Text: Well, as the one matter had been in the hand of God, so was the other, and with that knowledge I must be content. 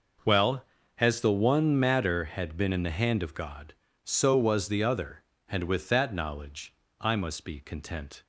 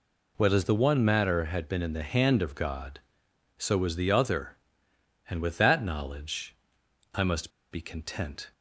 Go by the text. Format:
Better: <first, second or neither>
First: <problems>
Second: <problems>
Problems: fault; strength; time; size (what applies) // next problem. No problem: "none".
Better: first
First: pauses between "knowledge" and "I"; slight; at 6.7 s; 0.26 s long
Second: pauses between "knowledge" and "I"; noticeable; at 6.5 s; 0.58 s long // pauses between "must" and "be"; slight; at 7.5 s; 0.20 s long